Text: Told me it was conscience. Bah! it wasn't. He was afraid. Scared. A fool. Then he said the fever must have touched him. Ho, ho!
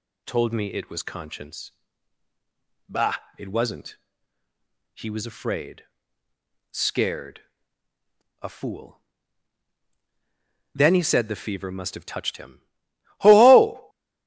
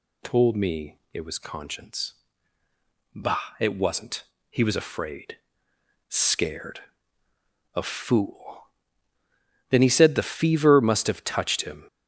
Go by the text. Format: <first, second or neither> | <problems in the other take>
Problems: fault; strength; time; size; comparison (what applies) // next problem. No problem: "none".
first | pauses between "me" and "it"; slight; at 0.9 s; 0.16 s long // stops before "Ho ho"; at 11.8 s